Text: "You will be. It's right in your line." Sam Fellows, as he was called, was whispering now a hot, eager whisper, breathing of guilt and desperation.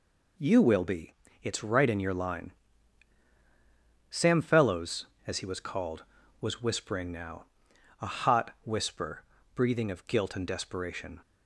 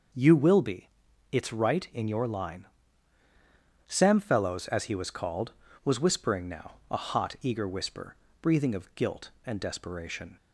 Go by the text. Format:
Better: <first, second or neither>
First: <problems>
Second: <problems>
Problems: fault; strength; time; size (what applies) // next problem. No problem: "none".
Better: second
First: pauses between "now" and "a"; noticeable; at 7.4 s; 0.56 s long // skips "eager"; at 8.5 s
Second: pauses between "now" and "a"; slight; at 6.7 s; 0.16 s long